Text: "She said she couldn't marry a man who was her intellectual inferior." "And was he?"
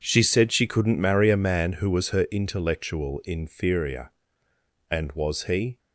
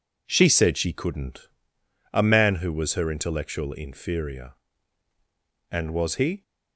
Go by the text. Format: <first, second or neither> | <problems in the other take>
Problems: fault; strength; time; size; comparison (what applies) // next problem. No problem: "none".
first | skips "marry"; at 1.8 s